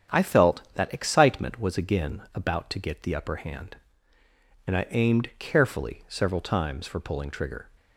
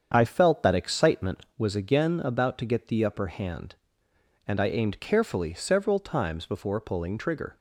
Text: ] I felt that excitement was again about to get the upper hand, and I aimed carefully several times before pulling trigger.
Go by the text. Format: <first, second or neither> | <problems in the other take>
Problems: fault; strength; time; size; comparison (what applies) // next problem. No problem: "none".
second | starts louder than the rest; strong; until 1.2 s; 8.5 dB; strong in the second // says "for" for "before"; at 6.8 s